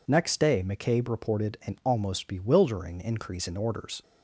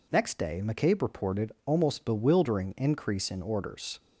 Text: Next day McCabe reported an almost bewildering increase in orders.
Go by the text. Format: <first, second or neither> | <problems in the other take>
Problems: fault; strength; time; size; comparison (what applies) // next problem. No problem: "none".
first | skips "an"; at 1.5 s